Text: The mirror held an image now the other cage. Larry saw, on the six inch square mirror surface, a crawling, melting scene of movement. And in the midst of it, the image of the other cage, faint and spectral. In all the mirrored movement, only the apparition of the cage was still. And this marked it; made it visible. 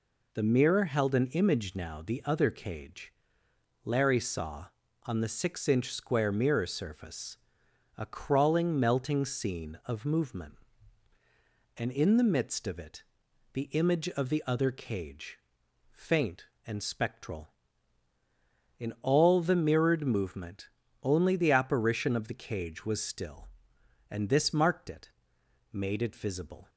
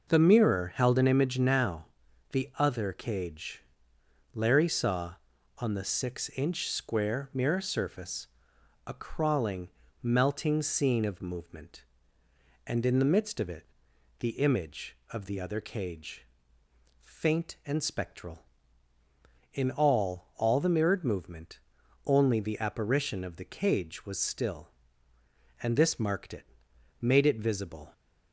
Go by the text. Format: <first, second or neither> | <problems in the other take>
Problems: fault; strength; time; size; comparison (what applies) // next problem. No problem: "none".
first | pauses between "now" and "the"; noticeable; at 1.8 s; 0.46 s long // says "all" twice; at 20.3 s